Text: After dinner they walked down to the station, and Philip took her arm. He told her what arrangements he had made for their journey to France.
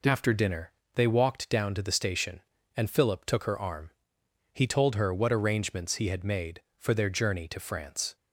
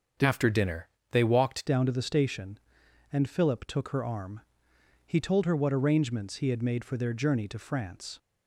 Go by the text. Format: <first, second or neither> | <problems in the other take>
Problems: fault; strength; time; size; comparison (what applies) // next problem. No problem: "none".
first | starts louder than the rest; until 1.4 s; 7 dB // pauses between "dinner" and "they"; slight; at 0.8 s; 0.22 s long; slight in the first // changes voice at "down"; from 1.6 s on; 6.5 s long